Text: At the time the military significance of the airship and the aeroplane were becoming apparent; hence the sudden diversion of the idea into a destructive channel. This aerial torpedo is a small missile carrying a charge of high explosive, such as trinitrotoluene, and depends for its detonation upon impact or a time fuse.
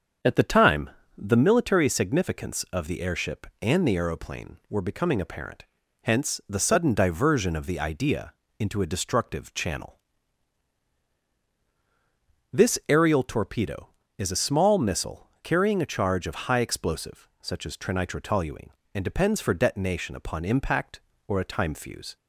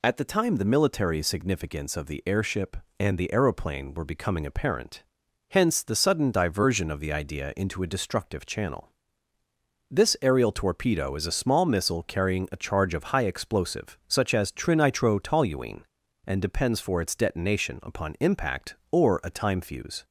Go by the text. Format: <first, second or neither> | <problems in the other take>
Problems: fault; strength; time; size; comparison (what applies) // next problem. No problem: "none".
second | starts louder than the rest; until 1.5 s; 7 dB // pauses between "time" and "the"; slight; at 0.8 s; 0.28 s long // pauses between "idea" and "into"; slight; at 8.3 s; 0.28 s long // skips "its"; at 19.5 s